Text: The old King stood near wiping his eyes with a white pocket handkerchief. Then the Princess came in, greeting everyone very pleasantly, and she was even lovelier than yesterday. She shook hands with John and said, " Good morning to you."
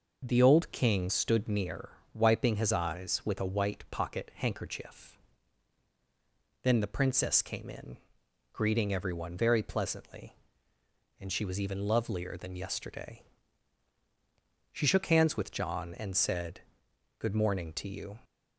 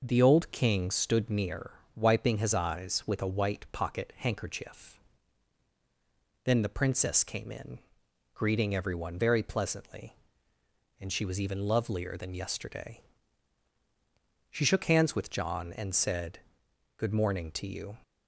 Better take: neither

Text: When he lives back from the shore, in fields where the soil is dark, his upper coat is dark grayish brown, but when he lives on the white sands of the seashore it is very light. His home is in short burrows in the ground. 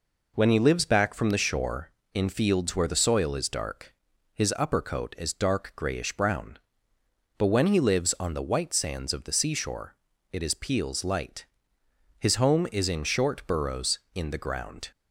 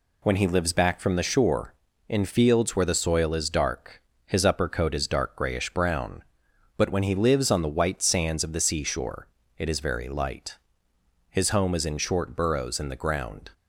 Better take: second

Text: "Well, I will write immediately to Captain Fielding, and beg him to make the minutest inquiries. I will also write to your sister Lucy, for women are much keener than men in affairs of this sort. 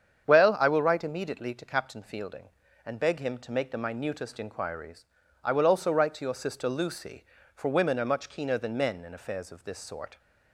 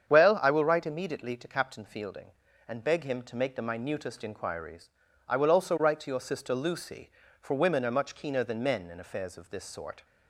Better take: neither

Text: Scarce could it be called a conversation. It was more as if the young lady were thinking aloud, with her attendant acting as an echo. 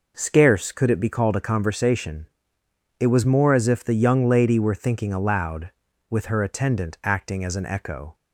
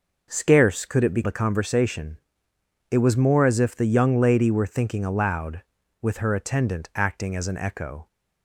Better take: first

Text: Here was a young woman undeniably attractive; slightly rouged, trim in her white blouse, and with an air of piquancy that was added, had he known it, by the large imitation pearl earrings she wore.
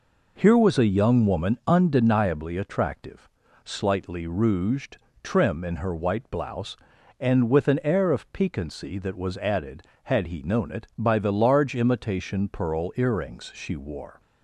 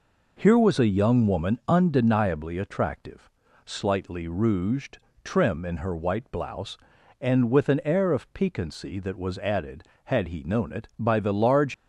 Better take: first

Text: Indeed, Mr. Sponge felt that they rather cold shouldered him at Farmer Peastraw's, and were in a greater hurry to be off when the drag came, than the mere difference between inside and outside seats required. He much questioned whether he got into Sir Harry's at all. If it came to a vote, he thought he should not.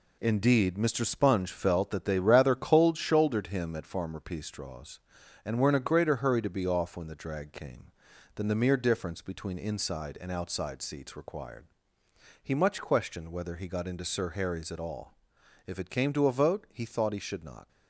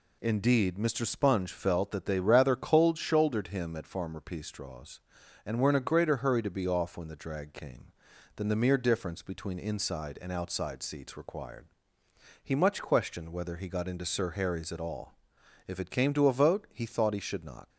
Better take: second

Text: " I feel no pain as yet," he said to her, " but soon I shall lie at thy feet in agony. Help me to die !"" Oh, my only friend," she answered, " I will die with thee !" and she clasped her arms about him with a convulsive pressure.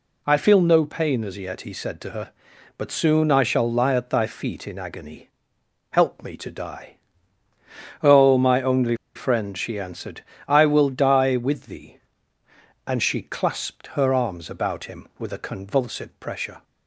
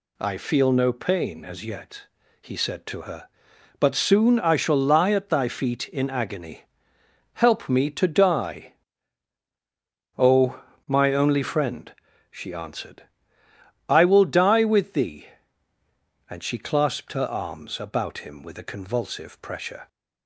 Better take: second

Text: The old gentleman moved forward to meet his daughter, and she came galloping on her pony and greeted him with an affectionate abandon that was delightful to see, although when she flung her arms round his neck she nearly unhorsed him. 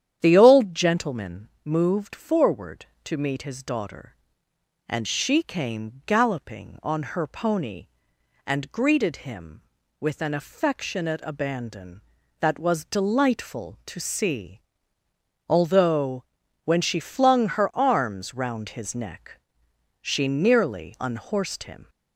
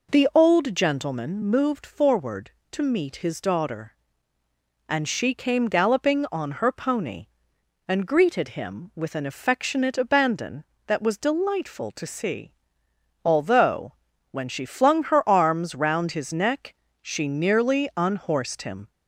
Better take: second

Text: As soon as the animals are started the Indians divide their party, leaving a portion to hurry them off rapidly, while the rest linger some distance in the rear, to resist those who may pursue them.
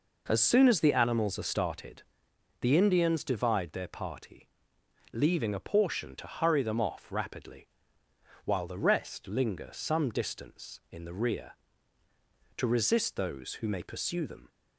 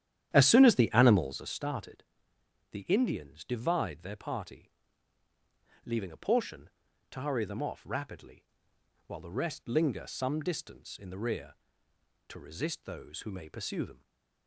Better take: first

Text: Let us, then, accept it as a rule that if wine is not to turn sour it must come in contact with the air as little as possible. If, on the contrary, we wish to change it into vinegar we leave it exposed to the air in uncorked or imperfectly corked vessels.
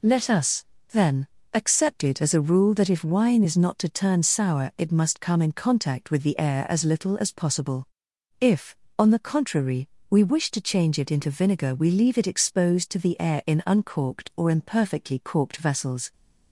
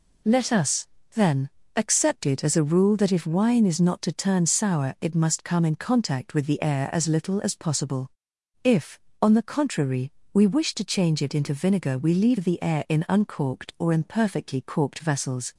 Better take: first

